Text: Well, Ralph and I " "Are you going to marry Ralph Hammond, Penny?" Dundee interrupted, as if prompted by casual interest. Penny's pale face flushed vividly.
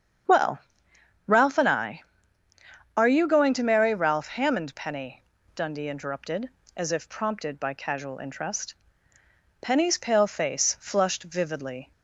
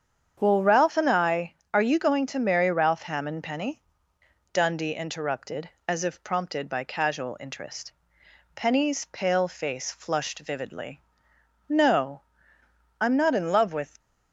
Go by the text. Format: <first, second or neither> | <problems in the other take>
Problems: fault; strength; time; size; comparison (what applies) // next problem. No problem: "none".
first | starts louder than the rest; strong; until 1.4 s; 8 dB; strong in the first // goes on to say "No I'm not in love with"; strong; from 11.6 s on; 2.3 s long